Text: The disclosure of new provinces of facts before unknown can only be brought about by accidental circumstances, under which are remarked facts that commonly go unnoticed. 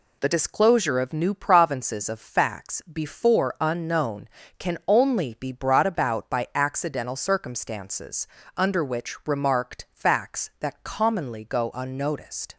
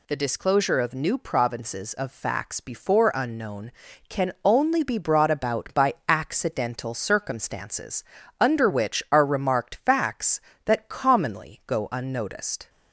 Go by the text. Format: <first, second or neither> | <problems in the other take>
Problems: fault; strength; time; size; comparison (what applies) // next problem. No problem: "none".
second | skips "are"; at 9.2 s